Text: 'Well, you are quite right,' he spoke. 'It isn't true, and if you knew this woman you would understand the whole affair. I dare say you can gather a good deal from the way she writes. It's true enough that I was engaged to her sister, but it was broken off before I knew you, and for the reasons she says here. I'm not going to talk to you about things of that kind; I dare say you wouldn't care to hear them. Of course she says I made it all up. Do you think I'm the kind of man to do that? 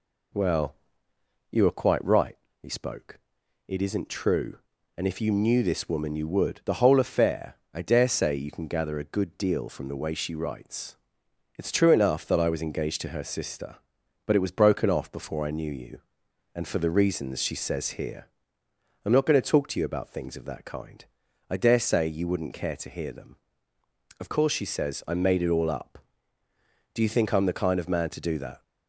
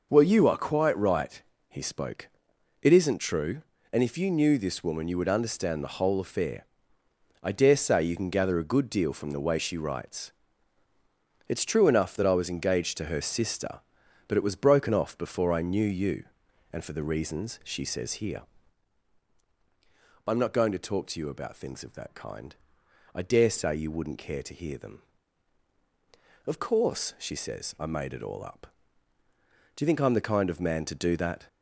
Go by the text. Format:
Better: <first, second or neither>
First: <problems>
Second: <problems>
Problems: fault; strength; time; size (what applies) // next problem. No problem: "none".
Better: second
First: skips "understand"; at 6.6 s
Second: none